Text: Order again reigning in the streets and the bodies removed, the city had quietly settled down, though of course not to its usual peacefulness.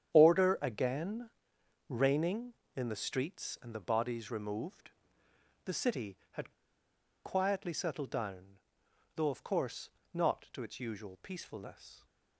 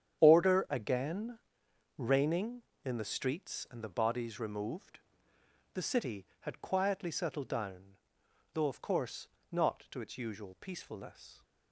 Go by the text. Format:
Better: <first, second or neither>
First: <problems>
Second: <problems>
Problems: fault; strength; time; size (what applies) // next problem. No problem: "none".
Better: second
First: starts louder than the rest; strong; until 1.1 s; 9 dB // pauses between "again" and "reigning"; noticeable; at 1.2 s; 0.62 s long // pauses between "had" and "quietly"; noticeable; at 6.5 s; 0.71 s long // pauses between "course" and "not"; slight; at 9.8 s; 0.24 s long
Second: starts louder than the rest; strong; until 1.2 s; 9 dB // pauses between "again" and "reigning"; noticeable; at 1.3 s; 0.62 s long // pauses between "course" and "not"; slight; at 9.2 s; 0.24 s long